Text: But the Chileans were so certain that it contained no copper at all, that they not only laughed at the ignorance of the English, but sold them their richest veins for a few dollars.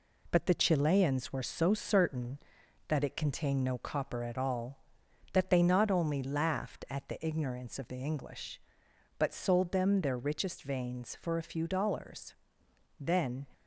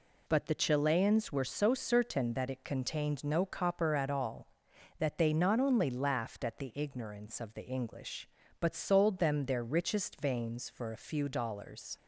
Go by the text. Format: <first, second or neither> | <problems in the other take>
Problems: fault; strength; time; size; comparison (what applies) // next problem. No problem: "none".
second | goes on to say "Then"; slight; from 12.9 s on; 0.48 s long